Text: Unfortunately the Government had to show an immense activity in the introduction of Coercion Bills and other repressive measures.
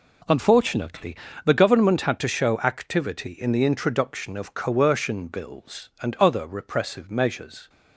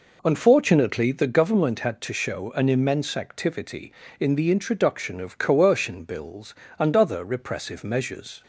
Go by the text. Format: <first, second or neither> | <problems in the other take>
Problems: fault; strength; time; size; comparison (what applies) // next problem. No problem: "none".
second | pauses between "Unfortunately" and "the"; slight; at 1.1 s; 0.28 s long // skips "an immense"; at 2.5 s